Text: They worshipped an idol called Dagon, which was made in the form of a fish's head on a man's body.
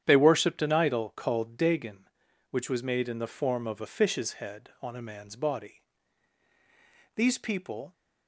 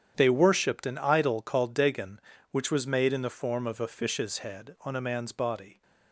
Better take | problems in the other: second | starts louder than the rest; strong; until 1.0 s; 9.5 dB; strong in the second // goes on to say "These people"; noticeable; from 7.1 s on; 0.78 s long

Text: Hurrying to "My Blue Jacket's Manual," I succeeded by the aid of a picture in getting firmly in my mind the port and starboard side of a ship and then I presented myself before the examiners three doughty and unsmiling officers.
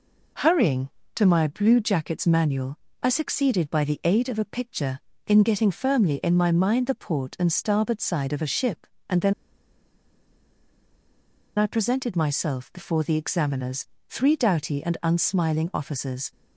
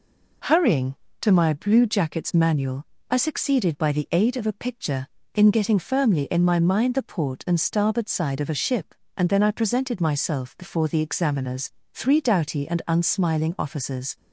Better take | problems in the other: second | pauses between "then" and "I"; strong; at 9.3 s; 2.2 s long // pauses between "examiners" and "three"; slight; at 13.8 s; 0.24 s long; slight in the second

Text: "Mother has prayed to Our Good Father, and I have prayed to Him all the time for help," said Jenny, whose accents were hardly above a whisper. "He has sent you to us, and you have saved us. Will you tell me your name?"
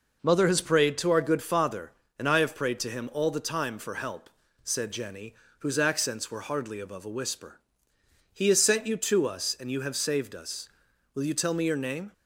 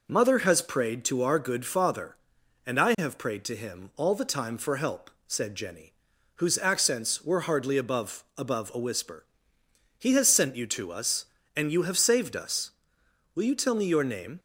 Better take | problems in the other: first | says "above" twice; at 8.3 s

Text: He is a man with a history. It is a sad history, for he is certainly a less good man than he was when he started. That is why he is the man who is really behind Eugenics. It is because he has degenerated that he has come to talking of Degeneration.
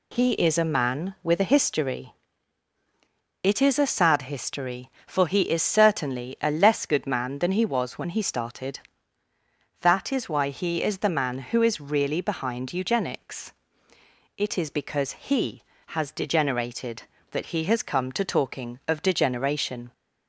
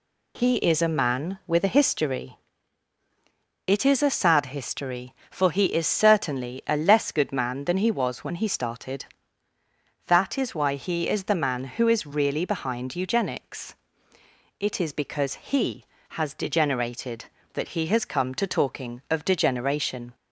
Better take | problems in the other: neither | none

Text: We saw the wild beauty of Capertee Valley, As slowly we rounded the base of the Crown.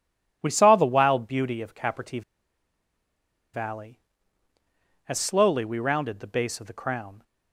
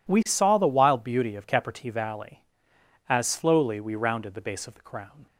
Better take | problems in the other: second | pauses between "Capertee" and "Valley"; strong; at 2.2 s; 1.3 s long

